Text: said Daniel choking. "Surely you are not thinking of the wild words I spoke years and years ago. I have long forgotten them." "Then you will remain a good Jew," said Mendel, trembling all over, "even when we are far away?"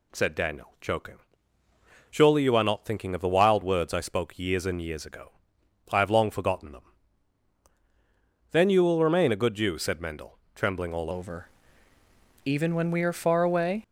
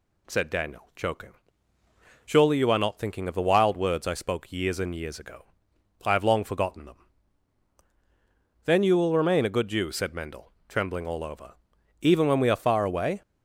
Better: second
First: changes voice at "over"; from 11.1 s on; 2.7 s long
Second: none

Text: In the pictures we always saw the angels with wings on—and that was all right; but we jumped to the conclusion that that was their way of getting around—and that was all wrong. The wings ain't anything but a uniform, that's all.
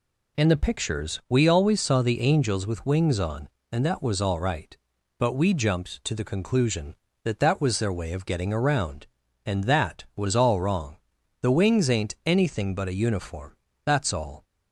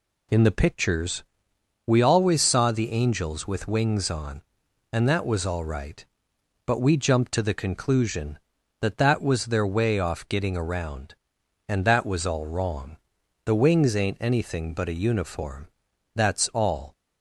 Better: first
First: none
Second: pauses between "pictures" and "we"; noticeable; at 1.2 s; 0.64 s long // says "off" for "of"; at 9.9 s

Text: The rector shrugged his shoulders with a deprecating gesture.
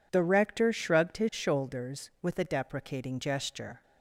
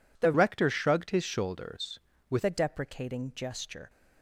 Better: first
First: none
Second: changes voice from "rector" to "with"; from 0.3 to 2.4 s; 2.1 s long

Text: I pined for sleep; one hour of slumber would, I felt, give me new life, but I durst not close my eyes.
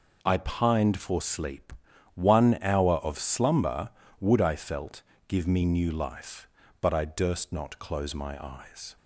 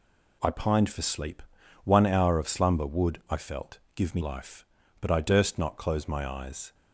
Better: first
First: none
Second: skips "new"; at 4.2 s

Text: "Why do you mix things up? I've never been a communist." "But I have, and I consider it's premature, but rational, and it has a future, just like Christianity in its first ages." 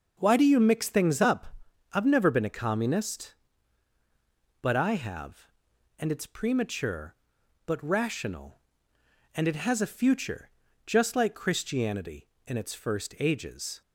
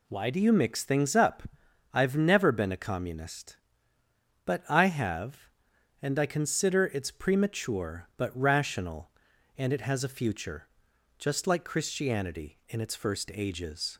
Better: second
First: skips "I consider"; at 6.1 s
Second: none

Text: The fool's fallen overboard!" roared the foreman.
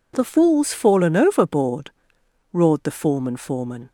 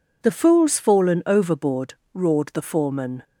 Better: second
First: says "foreman" twice; at 3.3 s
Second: none

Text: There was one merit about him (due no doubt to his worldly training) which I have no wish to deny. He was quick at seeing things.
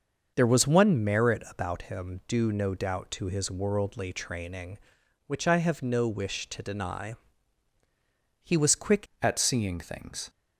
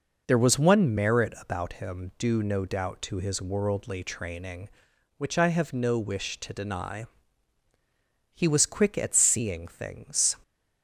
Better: second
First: starts louder than the rest; noticeable; until 1.3 s; 6 dB // changes voice at "at"; from 9.2 s on; 1.0 s long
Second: none

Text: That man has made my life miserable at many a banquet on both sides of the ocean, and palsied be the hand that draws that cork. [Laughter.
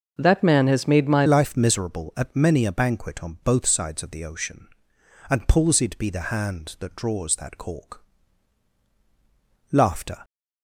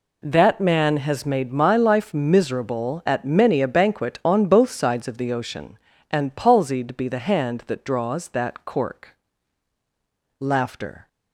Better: second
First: starts louder than the rest; noticeable; until 1.1 s; 6 dB // changes voice at "life"; from 1.2 s on; 9.0 s long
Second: none

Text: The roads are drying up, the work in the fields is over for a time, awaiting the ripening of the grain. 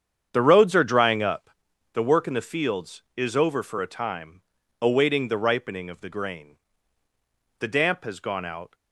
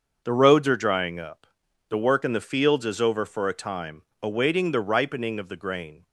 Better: second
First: starts louder than the rest; strong; until 1.3 s; 8 dB // goes on to say "The damp has gone out"; noticeable; from 7.6 s on; 1.1 s long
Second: starts louder than the rest; until 1.2 s; 6.5 dB

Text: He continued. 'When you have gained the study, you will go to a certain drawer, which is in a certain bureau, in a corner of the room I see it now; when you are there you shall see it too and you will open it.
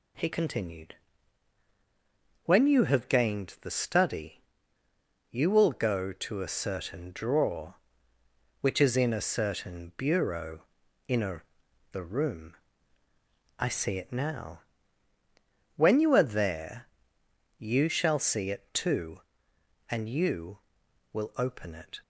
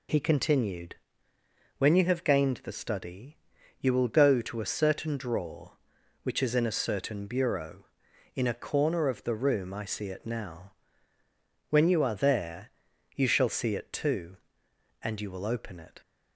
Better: second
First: skips "corner of"; at 11.6 s // pauses between "room" and "I"; at 12.5 s; 1.0 s long // pauses between "there" and "you"; noticeable; at 16.8 s; 0.72 s long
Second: pauses between "there" and "you"; at 12.7 s; 0.44 s long

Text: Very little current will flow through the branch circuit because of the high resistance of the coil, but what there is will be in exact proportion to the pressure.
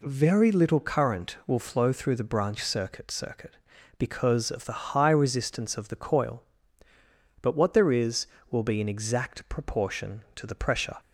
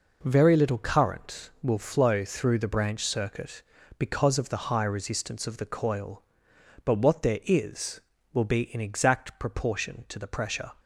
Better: second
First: says "circuit" twice; at 3.1 s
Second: none

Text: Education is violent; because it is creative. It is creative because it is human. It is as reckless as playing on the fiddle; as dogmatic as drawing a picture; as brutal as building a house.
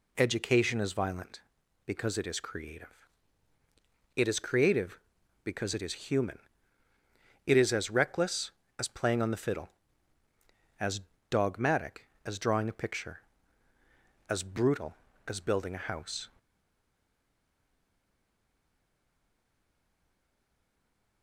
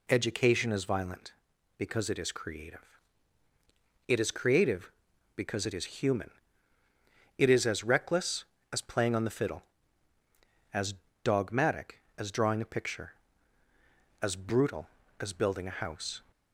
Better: second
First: pauses between "as" and "dogmatic"; slight; at 10.9 s; 0.32 s long // stays silent after the last word; strong; from 16.3 s on; 4.9 s long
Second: pauses between "as" and "dogmatic"; slight; at 10.9 s; 0.32 s long

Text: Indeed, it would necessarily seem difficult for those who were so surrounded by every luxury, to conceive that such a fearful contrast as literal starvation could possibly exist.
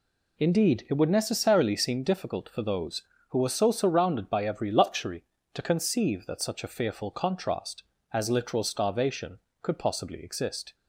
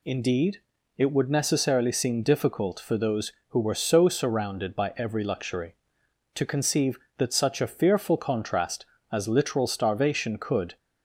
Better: first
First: none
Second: stops before "possibly exist"; at 10.7 s

